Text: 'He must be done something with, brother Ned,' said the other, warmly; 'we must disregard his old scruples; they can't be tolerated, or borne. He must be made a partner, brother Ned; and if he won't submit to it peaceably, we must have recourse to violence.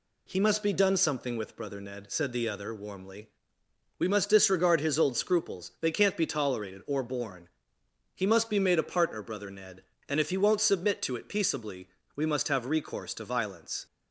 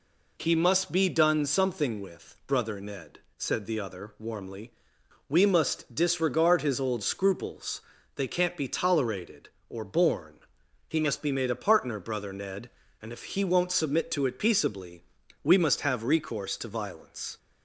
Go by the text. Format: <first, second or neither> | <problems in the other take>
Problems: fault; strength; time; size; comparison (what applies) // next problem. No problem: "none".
neither | none